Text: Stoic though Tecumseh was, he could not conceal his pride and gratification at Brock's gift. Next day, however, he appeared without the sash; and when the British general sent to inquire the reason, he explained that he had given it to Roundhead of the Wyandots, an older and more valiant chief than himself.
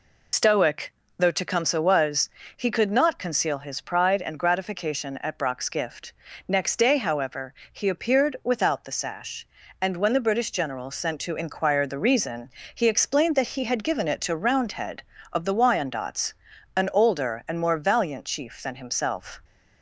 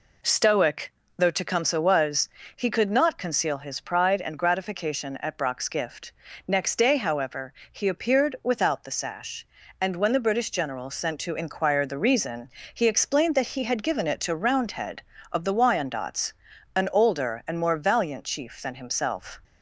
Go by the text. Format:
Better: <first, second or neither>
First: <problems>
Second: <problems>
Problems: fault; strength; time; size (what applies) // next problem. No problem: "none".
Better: second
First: loses the start of "Stoic"; at 0.3 s; 90 ms // pauses between "Stoic" and "though"; slight; at 0.9 s; 0.24 s long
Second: pauses between "Stoic" and "though"; slight; at 0.9 s; 0.24 s long